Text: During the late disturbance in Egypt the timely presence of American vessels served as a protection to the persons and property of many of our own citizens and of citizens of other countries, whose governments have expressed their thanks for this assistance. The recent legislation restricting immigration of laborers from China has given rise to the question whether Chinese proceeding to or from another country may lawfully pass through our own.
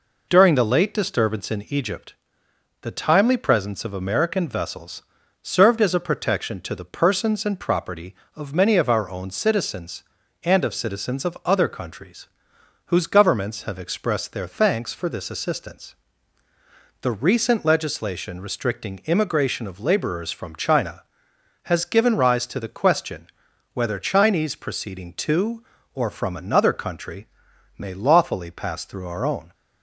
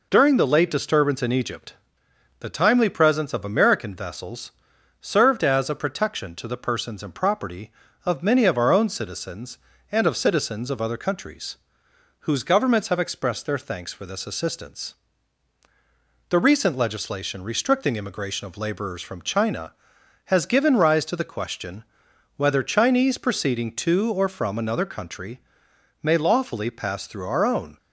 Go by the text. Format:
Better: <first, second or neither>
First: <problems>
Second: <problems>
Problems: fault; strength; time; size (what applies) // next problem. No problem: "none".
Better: neither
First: pauses between "Egypt" and "the"; noticeable; at 2.1 s; 0.68 s long // pauses between "vessels" and "served"; at 5.0 s; 0.40 s long // pauses between "question" and "whether"; noticeable; at 23.2 s; 0.46 s long // pauses between "country" and "may"; noticeable; at 27.2 s; 0.54 s long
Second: pauses between "Egypt" and "the"; noticeable; at 1.7 s; 0.64 s long // pauses between "vessels" and "served"; noticeable; at 4.5 s; 0.48 s long // pauses between "question" and "whether"; noticeable; at 21.8 s; 0.54 s long // pauses between "country" and "may"; noticeable; at 25.4 s; 0.60 s long